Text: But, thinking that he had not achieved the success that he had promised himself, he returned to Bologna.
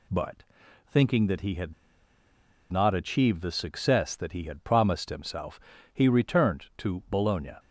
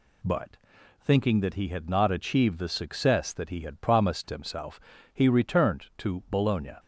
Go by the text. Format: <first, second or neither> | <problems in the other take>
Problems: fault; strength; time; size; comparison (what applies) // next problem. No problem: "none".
second | pauses between "had" and "not"; at 1.7 s; 0.98 s long